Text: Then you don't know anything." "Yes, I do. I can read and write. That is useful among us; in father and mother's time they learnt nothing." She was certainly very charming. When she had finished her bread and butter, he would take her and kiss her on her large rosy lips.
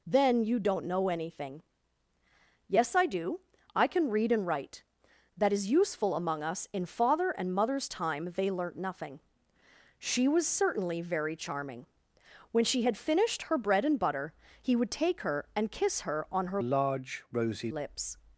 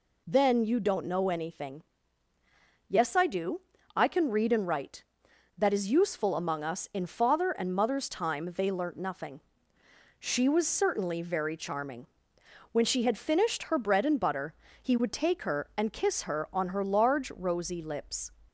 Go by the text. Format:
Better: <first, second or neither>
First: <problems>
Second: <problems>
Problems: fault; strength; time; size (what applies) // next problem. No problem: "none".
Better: second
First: changes voice from "large" to "rosy"; from 16.6 to 17.7 s; 1.1 s long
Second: none